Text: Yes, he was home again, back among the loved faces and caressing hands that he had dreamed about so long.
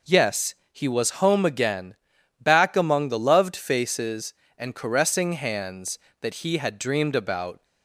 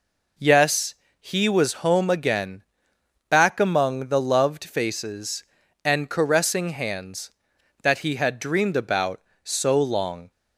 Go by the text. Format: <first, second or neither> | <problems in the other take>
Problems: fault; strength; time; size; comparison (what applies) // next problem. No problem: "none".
second | stops before "so long"; at 7.6 s